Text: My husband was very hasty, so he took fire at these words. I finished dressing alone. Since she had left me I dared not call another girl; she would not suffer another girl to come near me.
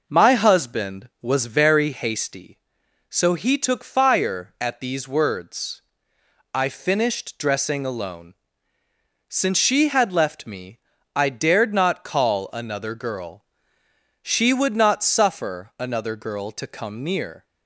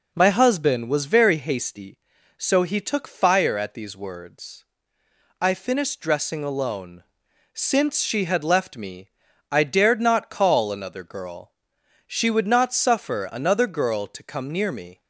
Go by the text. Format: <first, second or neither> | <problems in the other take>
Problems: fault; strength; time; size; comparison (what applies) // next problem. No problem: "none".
second | pauses between "me" and "I"; at 10.7 s; 0.38 s long; also in the second // stops before "me"; at 17.4 s